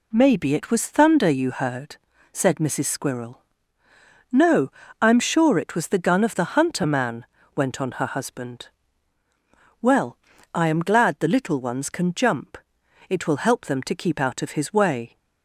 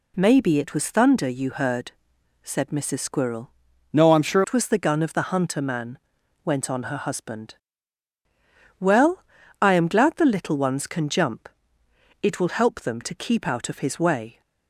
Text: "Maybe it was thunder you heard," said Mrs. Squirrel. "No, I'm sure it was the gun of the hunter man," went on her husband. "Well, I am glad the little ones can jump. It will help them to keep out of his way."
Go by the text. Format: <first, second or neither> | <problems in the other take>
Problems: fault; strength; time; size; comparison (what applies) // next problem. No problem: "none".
first | changes voice from "No" to "sure"; from 3.9 to 4.4 s; 0.5 s long